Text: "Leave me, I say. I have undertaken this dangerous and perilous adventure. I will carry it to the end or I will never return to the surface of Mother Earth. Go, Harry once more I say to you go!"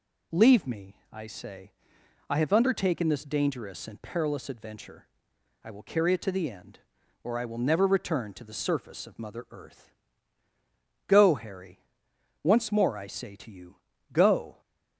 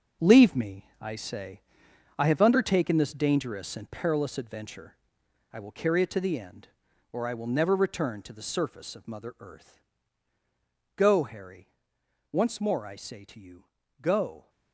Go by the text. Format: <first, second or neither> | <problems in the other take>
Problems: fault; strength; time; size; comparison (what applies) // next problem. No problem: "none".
first | gets quieter; strong; throughout; 9.5 dB // pauses between "Harry" and "once"; noticeable; at 11.6 s; 0.64 s long; noticeable in the first // pauses between "you" and "go"; slight; at 13.6 s; 0.34 s long; slight in the first